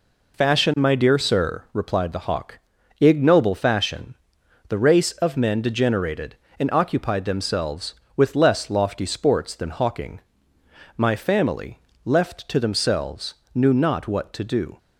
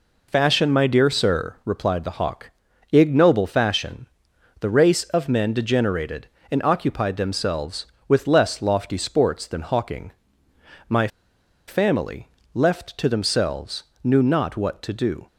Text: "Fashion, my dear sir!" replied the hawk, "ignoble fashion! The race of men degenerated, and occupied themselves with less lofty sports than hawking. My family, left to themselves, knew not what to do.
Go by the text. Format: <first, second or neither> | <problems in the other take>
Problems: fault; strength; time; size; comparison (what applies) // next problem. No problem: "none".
first | pauses between "My" and "family"; noticeable; at 11.0 s; 0.60 s long